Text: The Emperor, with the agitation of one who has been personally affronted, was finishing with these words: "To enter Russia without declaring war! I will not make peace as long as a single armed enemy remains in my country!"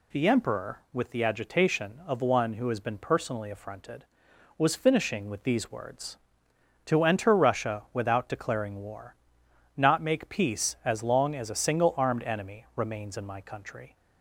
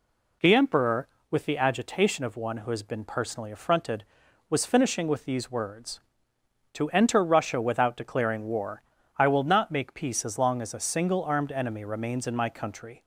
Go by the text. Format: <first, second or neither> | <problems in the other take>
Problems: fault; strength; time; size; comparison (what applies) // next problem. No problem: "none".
second | skips "I will"; at 9.4 s